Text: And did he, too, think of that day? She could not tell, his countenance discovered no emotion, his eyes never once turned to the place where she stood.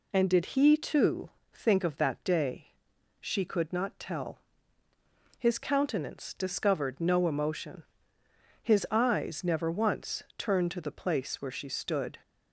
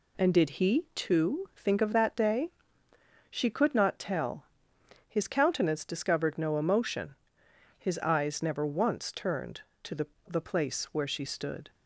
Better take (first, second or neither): first